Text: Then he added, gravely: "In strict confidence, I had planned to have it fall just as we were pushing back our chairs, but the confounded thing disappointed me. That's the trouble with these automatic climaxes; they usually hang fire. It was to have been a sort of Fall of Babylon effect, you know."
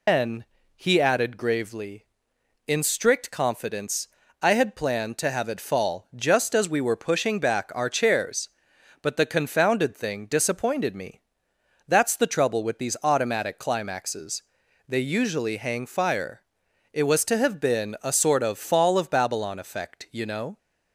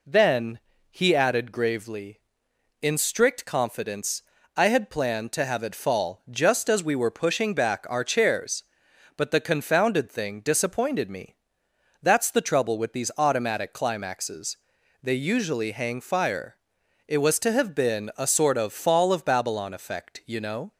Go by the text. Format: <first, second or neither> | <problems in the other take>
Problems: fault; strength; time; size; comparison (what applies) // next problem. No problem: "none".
second | loses the start of "Then"; at 0.0 s; 160 ms // pauses between "Then" and "he"; slight; at 0.4 s; 0.30 s long; slight in the second